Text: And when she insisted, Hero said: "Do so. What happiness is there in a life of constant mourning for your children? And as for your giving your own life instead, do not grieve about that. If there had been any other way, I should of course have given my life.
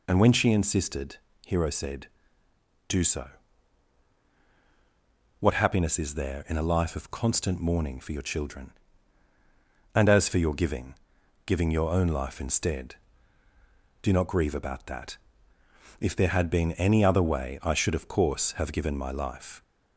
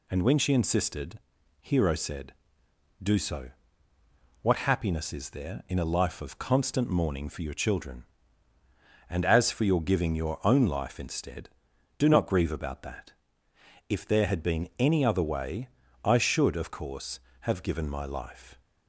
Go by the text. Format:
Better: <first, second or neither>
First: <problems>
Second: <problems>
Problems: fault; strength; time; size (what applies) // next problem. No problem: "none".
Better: second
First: says "giving" twice; at 11.4 s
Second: none